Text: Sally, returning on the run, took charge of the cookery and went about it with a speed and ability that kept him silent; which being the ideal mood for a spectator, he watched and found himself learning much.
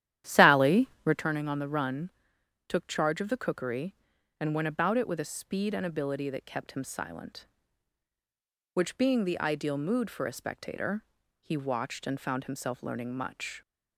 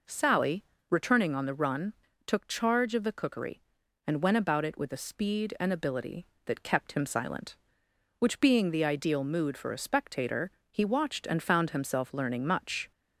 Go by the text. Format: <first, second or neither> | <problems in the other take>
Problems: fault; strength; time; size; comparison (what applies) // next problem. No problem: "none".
second | starts louder than the rest; strong; until 1.3 s; 11.5 dB